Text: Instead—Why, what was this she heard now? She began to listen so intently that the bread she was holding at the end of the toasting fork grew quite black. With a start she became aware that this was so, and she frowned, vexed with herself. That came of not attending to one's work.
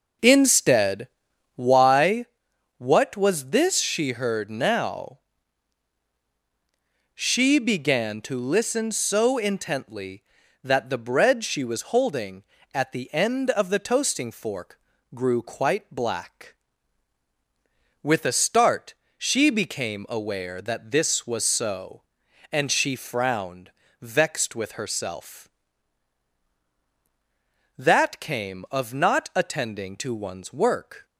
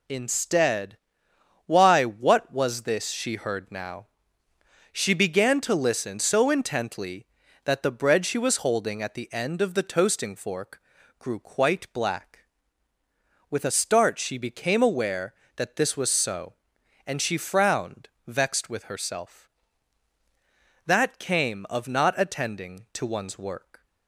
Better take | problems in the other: second | starts louder than the rest; noticeable; until 1.8 s; 5 dB // pauses between "fork" and "grew"; slight; at 14.7 s; 0.36 s long; also in the second // pauses between "start" and "she"; slight; at 18.9 s; 0.24 s long

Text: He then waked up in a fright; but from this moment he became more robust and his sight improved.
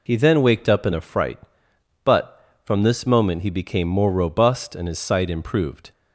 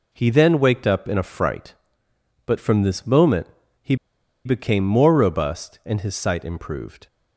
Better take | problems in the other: first | pauses between "moment" and "he"; slight; at 3.4 s; 0.34 s long // pauses between "he" and "became"; noticeable; at 3.9 s; 0.50 s long

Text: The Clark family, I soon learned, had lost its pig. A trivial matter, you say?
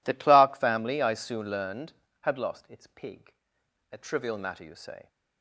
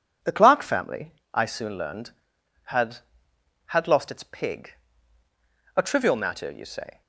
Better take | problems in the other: first | says "had" twice; at 3.6 s

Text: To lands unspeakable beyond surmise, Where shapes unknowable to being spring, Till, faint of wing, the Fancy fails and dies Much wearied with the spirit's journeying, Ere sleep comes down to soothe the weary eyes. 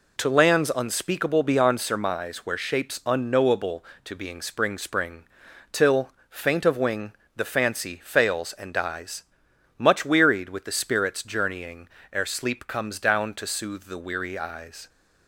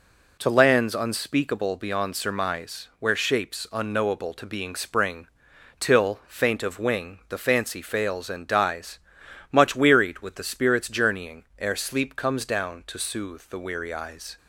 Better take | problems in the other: second | says "spring" twice; at 4.7 s // pauses between "dies" and "Much"; noticeable; at 9.2 s; 0.52 s long; noticeable in the second

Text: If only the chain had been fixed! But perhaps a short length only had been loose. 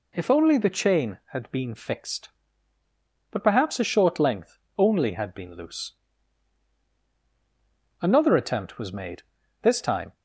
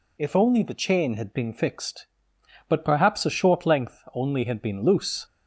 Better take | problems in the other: second | pauses between "length" and "only"; slight; at 4.5 s; 0.20 s long // goes on to say "Another attempt was made This time"; strong; from 7.9 s on; 2.1 s long

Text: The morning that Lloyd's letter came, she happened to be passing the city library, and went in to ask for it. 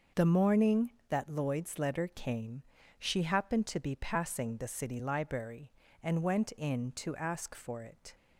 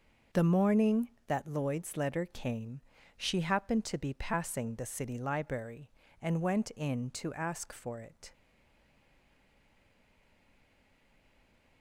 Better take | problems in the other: first | starts louder than the rest; noticeable; until 1.5 s; 6 dB; noticeable in the first // stays silent after the last word; strong; from 8.3 s on; 3.5 s long

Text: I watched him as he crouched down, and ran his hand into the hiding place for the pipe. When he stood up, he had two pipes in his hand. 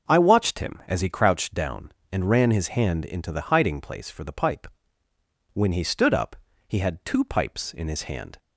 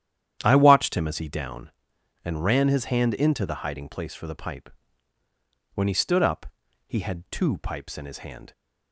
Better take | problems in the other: first | starts louder than the rest; strong; until 1.4 s; 10 dB; also in the first // skips "crouched"; at 1.2 s

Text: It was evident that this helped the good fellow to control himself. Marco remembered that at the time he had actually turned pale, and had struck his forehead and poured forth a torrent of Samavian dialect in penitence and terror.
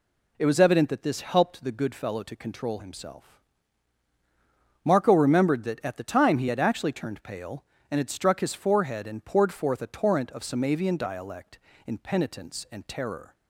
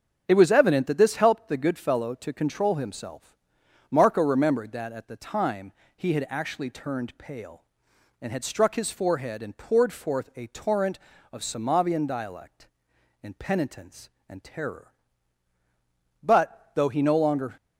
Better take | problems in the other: first | starts louder than the rest; strong; until 1.3 s; 7.5 dB // pauses between "time" and "he"; slight; at 5.7 s; 0.24 s long // goes on to say "But though he no longer"; from 16.2 s on; 1.3 s long

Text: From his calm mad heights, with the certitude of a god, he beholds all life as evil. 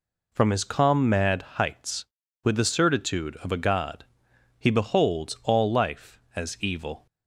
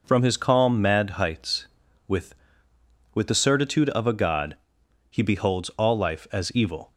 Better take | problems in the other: first | says "with" twice; at 3.1 s

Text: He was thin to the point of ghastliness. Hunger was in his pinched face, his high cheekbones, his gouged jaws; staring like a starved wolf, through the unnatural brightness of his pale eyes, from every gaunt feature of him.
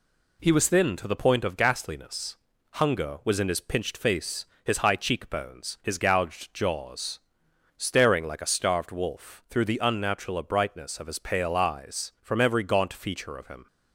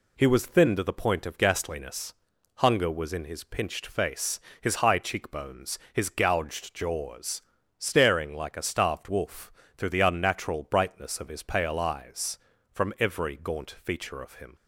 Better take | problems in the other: neither | none

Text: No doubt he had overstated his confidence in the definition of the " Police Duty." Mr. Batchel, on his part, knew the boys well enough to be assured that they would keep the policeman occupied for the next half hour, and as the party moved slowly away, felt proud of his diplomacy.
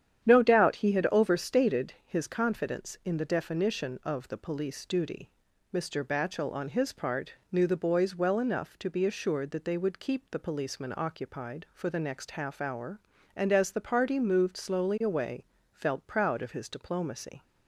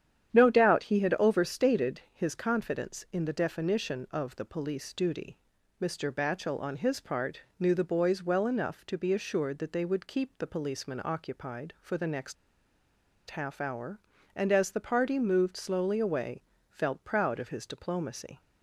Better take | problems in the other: first | starts louder than the rest; strong; until 1.3 s; 9.5 dB; strong in the first // pauses between "next" and "half"; noticeable; at 12.3 s; 0.94 s long

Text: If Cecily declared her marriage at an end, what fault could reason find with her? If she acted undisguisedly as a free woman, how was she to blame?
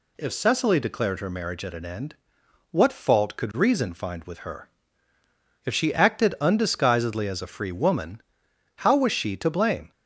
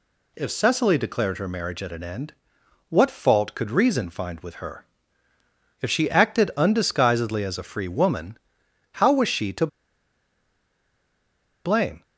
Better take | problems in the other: first | pauses between "to" and "blame"; strong; at 9.6 s; 1.9 s long

